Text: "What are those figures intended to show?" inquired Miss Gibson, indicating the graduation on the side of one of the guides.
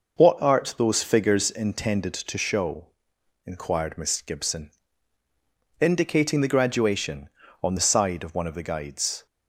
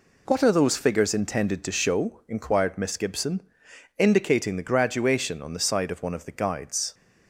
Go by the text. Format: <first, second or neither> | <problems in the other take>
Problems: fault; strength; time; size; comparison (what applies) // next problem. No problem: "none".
second | says "art" for "are"; at 0.4 s